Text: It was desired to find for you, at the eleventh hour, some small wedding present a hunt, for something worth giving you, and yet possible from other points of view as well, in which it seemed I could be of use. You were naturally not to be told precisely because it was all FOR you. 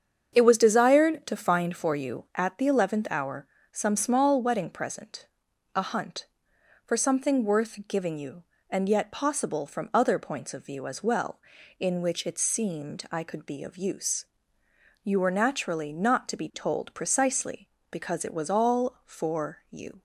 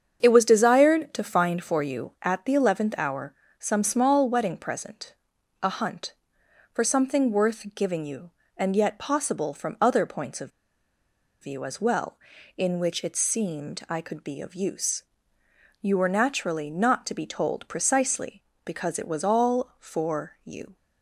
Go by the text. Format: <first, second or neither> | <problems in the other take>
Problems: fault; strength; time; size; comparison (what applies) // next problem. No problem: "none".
first | starts louder than the rest; strong; until 1.2 s; 7.5 dB; strong in the first // pauses between "present" and "a"; noticeable; at 5.1 s; 0.50 s long; noticeable in the first // pauses between "of" and "view"; noticeable; at 10.5 s; 0.92 s long